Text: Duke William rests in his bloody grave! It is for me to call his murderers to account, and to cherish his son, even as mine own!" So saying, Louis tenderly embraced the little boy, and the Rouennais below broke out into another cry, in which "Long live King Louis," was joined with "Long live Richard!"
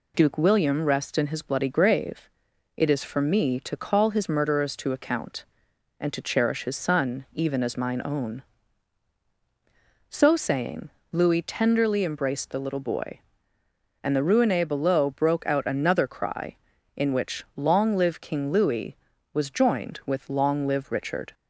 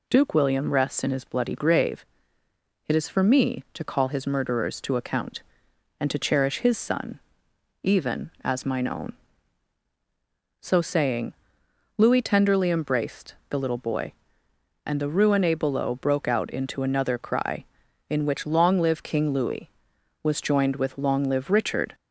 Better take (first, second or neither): second